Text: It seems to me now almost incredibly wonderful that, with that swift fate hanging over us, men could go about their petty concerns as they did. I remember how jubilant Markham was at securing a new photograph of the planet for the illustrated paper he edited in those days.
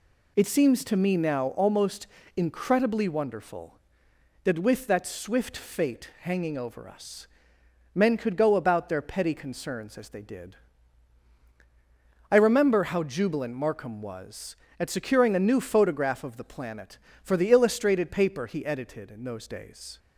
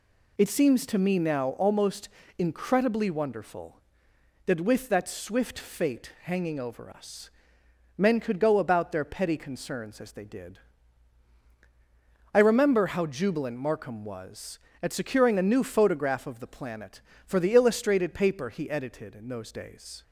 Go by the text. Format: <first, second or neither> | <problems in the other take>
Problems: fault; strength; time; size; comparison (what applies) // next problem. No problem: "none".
neither | pauses between "almost" and "incredibly"; slight; the same in both